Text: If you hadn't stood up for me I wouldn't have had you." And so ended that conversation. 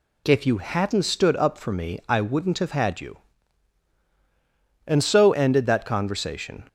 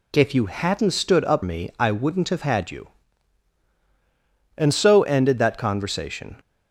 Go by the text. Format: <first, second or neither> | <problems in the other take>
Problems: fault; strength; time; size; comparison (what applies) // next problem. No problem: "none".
first | skips "for"; at 1.4 s